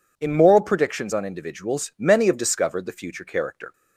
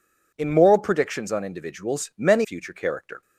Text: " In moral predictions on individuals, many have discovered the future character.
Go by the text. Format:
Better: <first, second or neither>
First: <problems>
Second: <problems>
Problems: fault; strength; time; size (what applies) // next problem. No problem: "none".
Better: first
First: none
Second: skips "have discovered the"; at 2.4 s